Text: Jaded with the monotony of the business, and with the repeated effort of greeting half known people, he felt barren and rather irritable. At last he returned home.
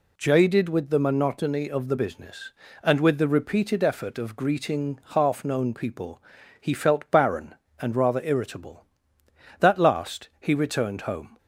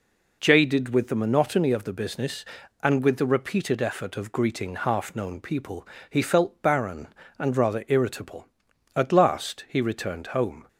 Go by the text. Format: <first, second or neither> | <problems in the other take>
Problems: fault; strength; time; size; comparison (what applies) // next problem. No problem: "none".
second | says "That" for "At"; at 9.5 s